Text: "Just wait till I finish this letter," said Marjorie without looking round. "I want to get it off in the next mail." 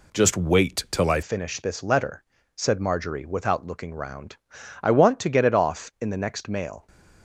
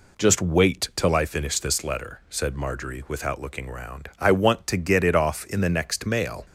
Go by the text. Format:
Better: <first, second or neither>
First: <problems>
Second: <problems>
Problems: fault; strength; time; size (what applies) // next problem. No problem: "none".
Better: second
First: changes voice at "finish"; from 1.2 s on; 5.6 s long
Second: none